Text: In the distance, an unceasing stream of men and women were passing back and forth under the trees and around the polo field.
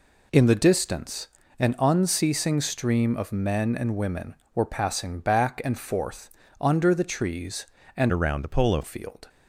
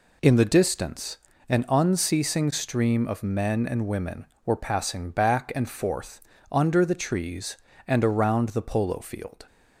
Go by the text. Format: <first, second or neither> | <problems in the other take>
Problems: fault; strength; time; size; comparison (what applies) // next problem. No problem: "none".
second | pauses between "forth" and "under"; slight; at 6.2 s; 0.32 s long; slight in the second // changes voice from "around" to "polo"; from 8.1 to 8.8 s; 0.7 s long